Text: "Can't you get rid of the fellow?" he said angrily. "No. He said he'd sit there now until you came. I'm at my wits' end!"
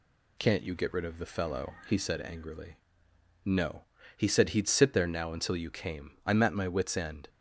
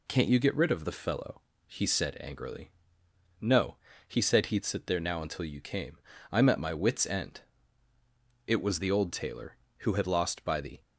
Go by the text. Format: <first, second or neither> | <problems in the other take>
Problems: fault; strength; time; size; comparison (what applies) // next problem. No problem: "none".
first | goes on to say "It was the old tailor who had lost by the"; strong; from 8.4 s on; 2.3 s long